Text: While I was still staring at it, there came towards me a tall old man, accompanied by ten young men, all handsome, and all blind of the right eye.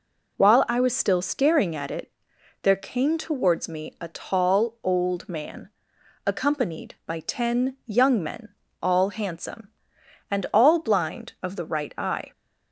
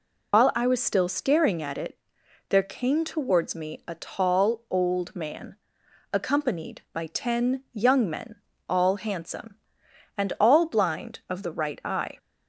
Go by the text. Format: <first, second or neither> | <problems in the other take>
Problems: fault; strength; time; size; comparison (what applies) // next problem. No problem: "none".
first | loses the start of "While"; at 0.3 s; 95 ms